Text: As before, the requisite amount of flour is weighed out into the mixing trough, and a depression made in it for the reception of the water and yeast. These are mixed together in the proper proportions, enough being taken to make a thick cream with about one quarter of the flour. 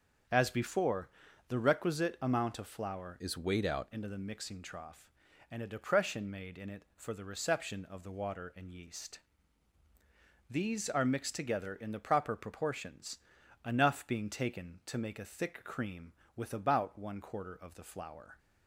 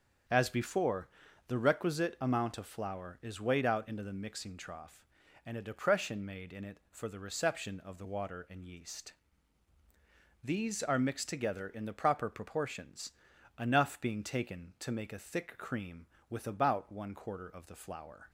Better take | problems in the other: second | starts louder than the rest; until 1.6 s; 6.5 dB; also in the second // changes voice from "is" to "out"; from 3.1 to 3.8 s; 0.7 s long

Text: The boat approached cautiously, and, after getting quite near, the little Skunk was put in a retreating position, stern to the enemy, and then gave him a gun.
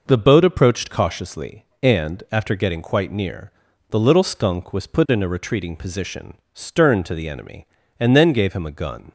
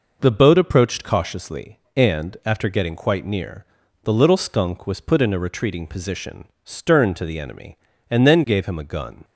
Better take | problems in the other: neither | none

